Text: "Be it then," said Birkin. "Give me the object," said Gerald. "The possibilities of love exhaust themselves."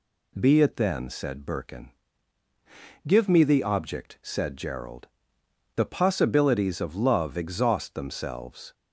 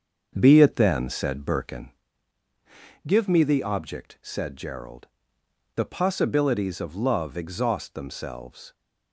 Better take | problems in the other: first | starts louder than the rest; until 2.1 s; 7 dB

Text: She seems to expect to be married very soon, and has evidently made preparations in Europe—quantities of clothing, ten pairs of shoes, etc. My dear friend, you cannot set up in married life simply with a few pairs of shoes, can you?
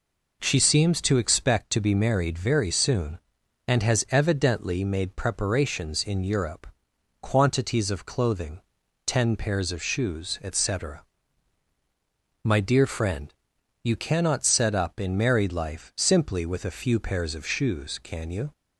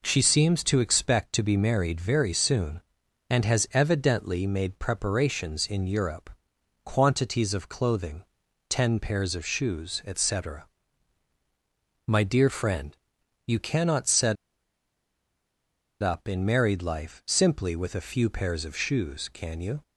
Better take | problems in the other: first | pauses between "set" and "up"; strong; at 14.3 s; 1.6 s long

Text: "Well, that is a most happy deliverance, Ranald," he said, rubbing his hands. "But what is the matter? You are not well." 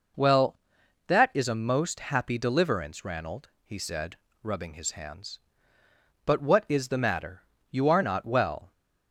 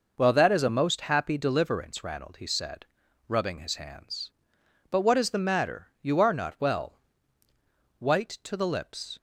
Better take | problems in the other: first | goes on to say "White to the lips"; noticeable; from 7.9 s on; 1.2 s long

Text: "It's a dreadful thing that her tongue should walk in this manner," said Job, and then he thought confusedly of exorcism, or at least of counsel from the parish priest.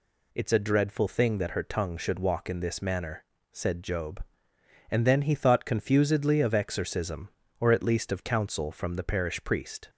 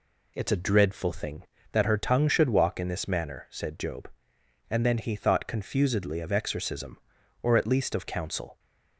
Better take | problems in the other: first | stops before "from the parish priest"; at 8.5 s

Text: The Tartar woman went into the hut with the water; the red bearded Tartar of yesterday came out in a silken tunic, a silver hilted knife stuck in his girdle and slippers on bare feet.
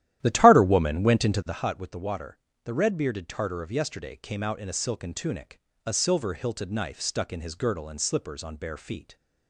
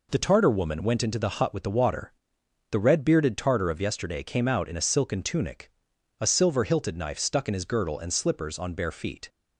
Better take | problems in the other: second | starts louder than the rest; strong; until 1.7 s; 12.5 dB

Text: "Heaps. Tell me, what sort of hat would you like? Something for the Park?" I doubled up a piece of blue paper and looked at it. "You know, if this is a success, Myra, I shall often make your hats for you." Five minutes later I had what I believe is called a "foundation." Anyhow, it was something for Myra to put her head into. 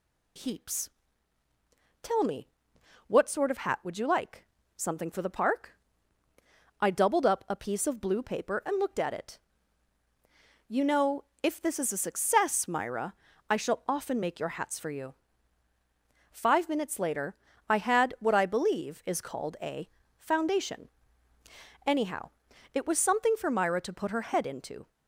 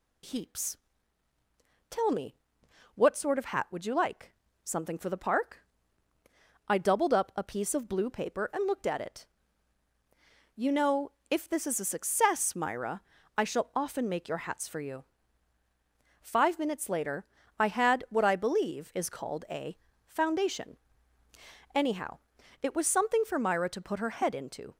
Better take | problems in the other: neither | pauses between "later" and "I"; slight; the same in both // pauses between "a" and "foundation"; slight; the same in both

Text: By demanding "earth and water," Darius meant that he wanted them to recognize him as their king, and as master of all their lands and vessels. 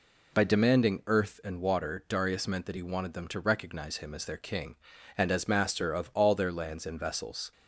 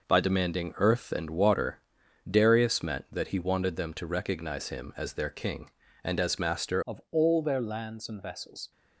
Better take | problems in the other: first | changes voice at "of"; from 6.8 s on; 1.9 s long

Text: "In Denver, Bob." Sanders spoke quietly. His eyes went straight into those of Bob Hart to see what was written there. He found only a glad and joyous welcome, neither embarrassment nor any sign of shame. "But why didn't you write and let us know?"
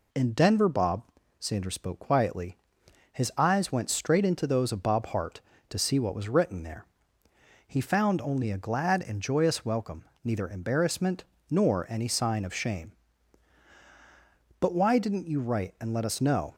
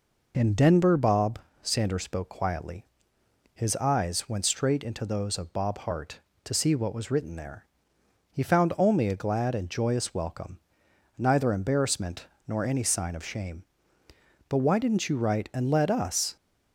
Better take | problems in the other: first | pauses between "embarrassment" and "nor"; slight; at 12.2 s; 0.20 s long; slight in the first // stops before "know"; at 16.3 s

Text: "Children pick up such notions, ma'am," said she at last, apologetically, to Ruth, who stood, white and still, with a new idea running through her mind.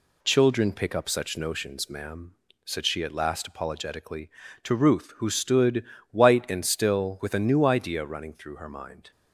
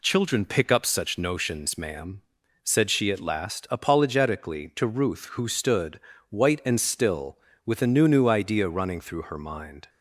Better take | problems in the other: first | says "new" twice; at 8.0 s

